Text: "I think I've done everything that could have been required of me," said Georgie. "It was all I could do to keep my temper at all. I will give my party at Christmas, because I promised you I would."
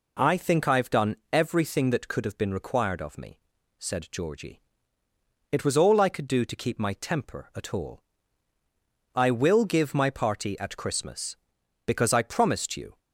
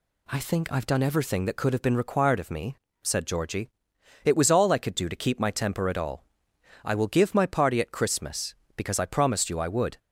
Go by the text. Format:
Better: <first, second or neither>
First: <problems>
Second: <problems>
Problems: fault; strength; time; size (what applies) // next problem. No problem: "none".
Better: second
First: pauses between "done" and "everything"; slight; at 1.1 s; 0.16 s long // stops before "I would"; at 12.9 s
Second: none